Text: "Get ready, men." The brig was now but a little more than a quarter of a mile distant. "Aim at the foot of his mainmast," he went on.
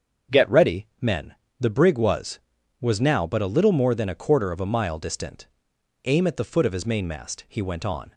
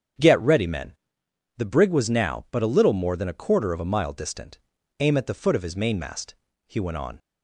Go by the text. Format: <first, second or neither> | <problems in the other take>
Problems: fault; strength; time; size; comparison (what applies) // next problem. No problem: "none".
second | starts louder than the rest; strong; until 1.7 s; 7 dB; strong in the second // says "was" twice; at 2.7 s